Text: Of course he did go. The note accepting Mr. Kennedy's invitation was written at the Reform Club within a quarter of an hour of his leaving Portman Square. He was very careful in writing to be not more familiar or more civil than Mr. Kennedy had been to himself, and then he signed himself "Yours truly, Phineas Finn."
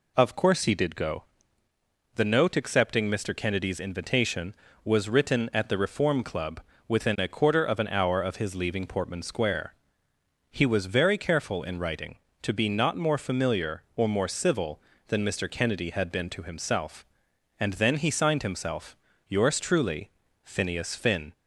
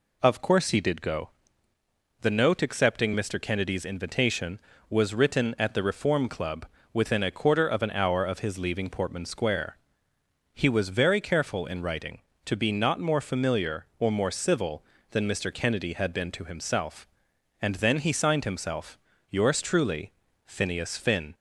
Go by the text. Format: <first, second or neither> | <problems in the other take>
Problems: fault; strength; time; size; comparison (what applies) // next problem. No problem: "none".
neither | pauses between "Club" and "within"; slight; the same in both // pauses between "himself" and "Yours"; slight; the same in both